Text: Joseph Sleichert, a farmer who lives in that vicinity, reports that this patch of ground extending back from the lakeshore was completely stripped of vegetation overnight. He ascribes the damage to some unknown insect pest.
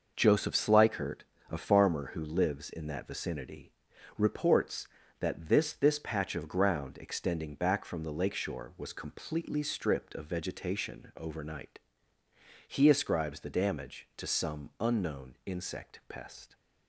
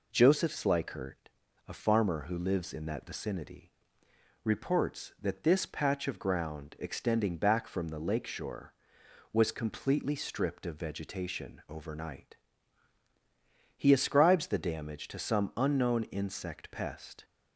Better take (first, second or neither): second